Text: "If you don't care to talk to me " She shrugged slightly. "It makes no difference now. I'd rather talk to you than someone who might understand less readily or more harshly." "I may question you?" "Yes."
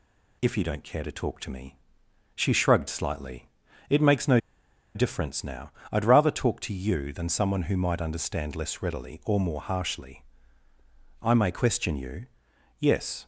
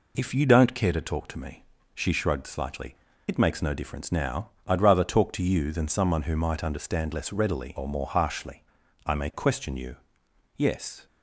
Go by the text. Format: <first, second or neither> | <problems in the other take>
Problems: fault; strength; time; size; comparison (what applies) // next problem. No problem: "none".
second | pauses between "no" and "difference"; noticeable; at 4.3 s; 0.56 s long